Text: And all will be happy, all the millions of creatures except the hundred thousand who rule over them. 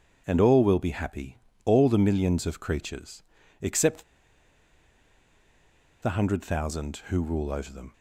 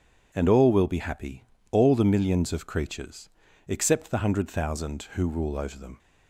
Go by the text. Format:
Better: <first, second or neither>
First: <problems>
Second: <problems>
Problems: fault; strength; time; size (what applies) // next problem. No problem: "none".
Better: second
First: pauses between "creatures" and "except"; at 3.2 s; 0.38 s long // pauses between "except" and "the"; strong; at 4.0 s; 1.9 s long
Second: pauses between "creatures" and "except"; at 3.2 s; 0.38 s long